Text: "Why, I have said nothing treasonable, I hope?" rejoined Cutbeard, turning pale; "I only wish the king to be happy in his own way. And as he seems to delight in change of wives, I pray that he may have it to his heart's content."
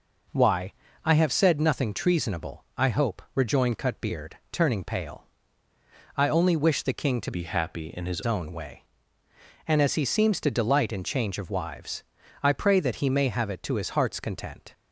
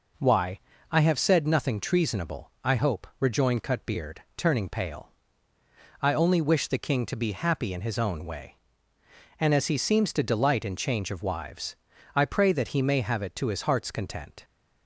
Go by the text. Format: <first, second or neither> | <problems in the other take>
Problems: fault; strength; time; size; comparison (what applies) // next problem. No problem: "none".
second | changes voice from "be" to "his"; from 7.3 to 8.2 s; 0.9 s long